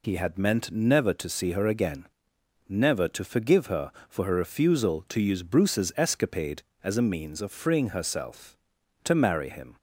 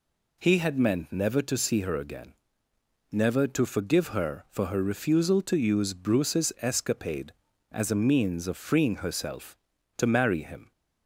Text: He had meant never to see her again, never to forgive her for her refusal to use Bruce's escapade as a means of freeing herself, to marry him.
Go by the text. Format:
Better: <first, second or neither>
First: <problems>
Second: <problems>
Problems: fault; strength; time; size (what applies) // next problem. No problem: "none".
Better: neither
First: none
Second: none